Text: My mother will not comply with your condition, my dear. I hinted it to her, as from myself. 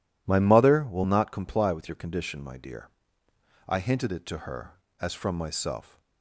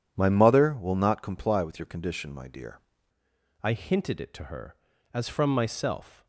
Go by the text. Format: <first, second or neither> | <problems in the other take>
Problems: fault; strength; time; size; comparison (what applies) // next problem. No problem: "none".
first | changes voice at "I"; from 3.6 s on; 2.6 s long